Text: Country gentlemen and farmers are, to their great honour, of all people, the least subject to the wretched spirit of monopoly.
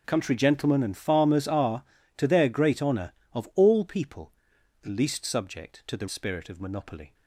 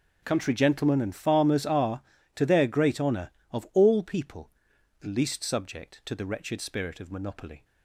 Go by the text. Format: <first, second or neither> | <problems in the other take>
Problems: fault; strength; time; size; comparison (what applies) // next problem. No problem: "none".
second | starts louder than the rest; noticeable; until 1.0 s; 6 dB; noticeable in the second // skips "wretched"; at 6.0 s